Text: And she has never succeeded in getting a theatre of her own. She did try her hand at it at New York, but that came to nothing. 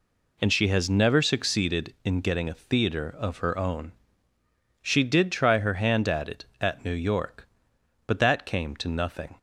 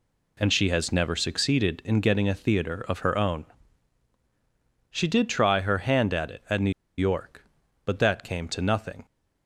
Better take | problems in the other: first | pauses between "New" and "York"; slight; at 6.7 s; 0.27 s long

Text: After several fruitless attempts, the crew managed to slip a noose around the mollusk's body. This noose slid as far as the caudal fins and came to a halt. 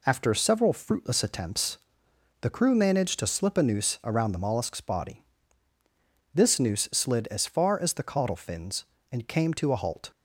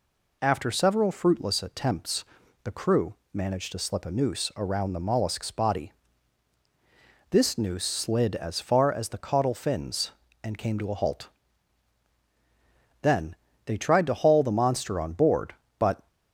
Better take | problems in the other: first | pauses between "crew" and "managed"; slight; at 3.1 s; 0.18 s long // goes on to say "Then they tried to haul the monster on board but"; strong; from 13.0 s on; 3.0 s long

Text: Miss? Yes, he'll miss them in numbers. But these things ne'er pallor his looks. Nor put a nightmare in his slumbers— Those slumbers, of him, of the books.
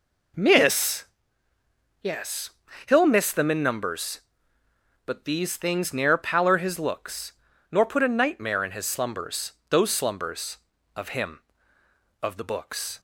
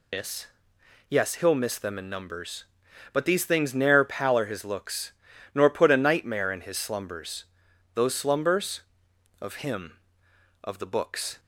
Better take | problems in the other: first | loses the start of "Miss"; at 0.1 s; 120 ms

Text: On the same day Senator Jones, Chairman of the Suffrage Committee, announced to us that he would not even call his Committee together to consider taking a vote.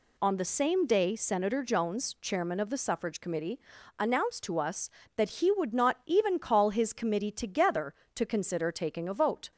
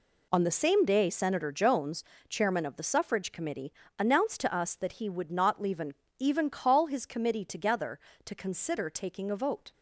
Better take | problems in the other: first | says "even" twice; at 6.1 s

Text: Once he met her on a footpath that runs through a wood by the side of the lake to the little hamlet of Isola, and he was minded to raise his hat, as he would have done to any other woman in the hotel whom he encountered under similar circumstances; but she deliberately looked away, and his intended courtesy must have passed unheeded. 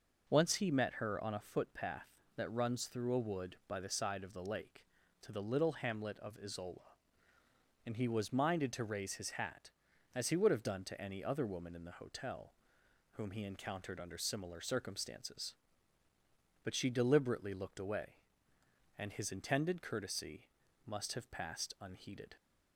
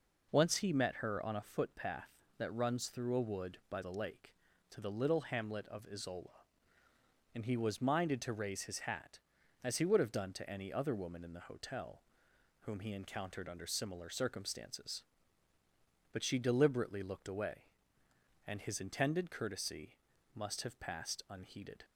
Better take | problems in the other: first | skips "the side of"; at 3.8 s // pauses between "hotel" and "whom"; noticeable; at 12.0 s; 0.58 s long; noticeable in the first // pauses between "courtesy" and "must"; at 19.9 s; 0.40 s long; also in the first

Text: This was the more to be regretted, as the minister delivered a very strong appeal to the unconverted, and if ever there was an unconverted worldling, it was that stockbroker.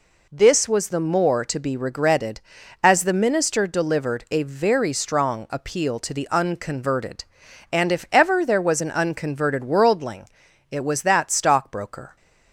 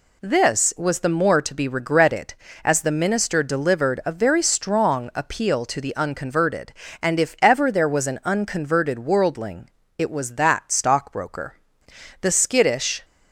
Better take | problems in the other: first | goes on to say "The skittish"; noticeable; from 12.2 s on; 0.84 s long

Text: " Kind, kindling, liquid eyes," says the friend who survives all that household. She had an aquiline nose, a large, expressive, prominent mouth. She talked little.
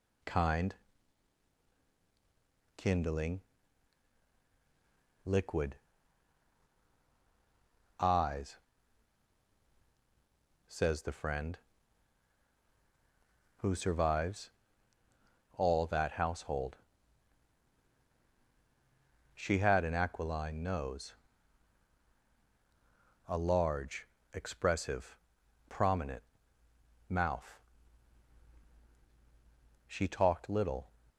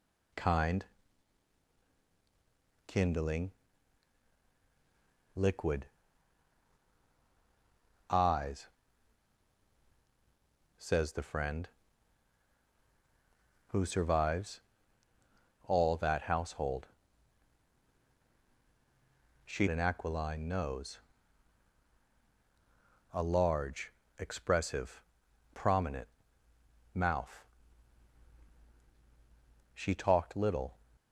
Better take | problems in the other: first | pauses between "liquid" and "eyes"; strong; at 5.8 s; 2.2 s long; strong in the first // pauses between "survives" and "all"; at 14.6 s; 1.0 s long; also in the first // skips "had"; at 19.6 s // pauses between "prominent" and "mouth"; noticeable; at 26.0 s; 0.84 s long; noticeable in the first

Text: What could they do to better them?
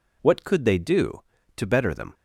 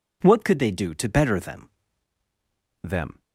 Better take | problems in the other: first | says "them" twice; at 2.8 s

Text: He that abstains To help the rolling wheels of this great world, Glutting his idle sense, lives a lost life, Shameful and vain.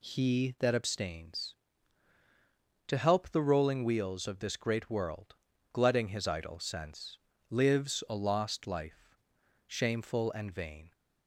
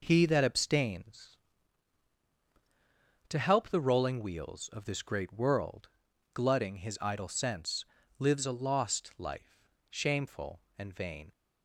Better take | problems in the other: neither | none

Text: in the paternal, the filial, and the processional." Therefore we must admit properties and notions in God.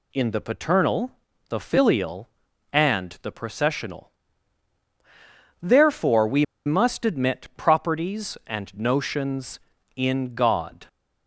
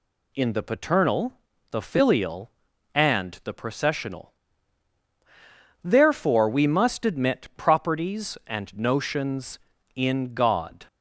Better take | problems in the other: second | pauses between "we" and "must"; slight; at 6.4 s; 0.21 s long

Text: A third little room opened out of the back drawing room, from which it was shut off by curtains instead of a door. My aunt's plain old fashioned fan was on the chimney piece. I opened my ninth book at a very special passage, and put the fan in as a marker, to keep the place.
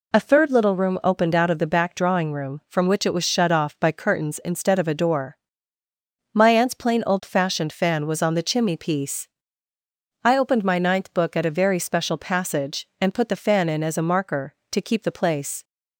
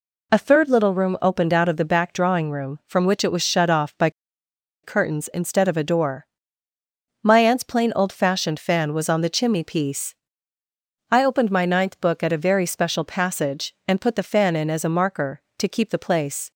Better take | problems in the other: first | pauses between "by" and "curtains"; noticeable; at 4.0 s; 0.73 s long

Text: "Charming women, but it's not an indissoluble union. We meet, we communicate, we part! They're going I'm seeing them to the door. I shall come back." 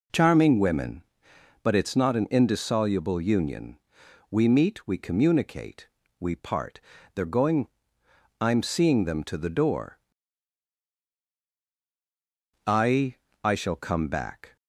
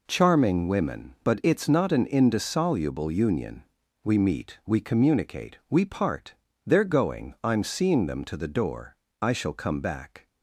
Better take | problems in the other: second | pauses between "going" and "I'm"; noticeable; at 7.6 s; 0.72 s long // says "I" twice; at 13.4 s

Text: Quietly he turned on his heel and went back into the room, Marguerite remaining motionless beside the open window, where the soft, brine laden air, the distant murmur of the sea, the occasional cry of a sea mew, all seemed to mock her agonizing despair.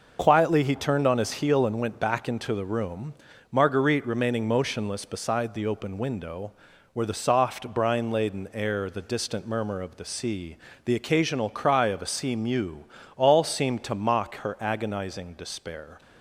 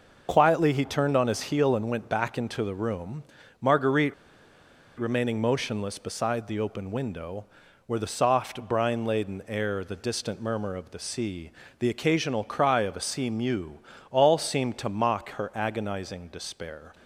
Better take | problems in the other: first | pauses between "Marguerite" and "remaining"; noticeable; at 4.1 s; 0.84 s long

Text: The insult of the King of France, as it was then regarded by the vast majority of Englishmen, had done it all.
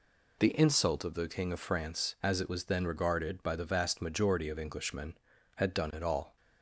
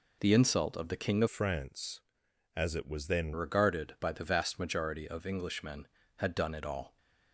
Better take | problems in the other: first | changes voice from "France" to "then"; from 1.2 to 3.3 s; 2.1 s long

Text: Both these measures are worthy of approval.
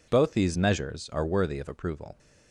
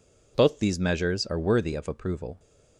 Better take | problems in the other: neither | none

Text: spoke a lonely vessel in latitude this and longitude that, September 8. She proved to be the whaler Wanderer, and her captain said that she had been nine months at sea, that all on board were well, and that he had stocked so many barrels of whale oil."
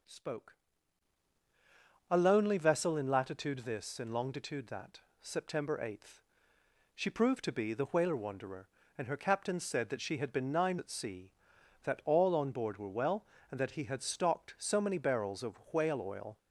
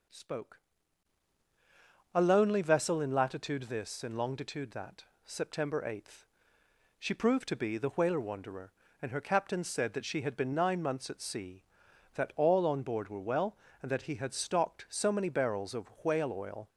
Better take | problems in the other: second | pauses between "spoke" and "a"; strong; at 0.5 s; 1.5 s long; strong in the second // skips "months"; at 10.7 s

